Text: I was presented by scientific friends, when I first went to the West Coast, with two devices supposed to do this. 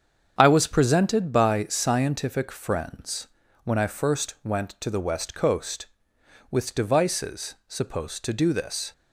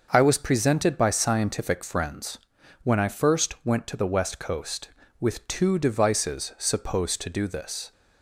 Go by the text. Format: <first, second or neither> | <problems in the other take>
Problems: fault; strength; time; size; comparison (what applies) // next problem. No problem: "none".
second | starts louder than the rest; strong; until 1.3 s; 7.5 dB; also in the second // skips "two"; at 6.7 s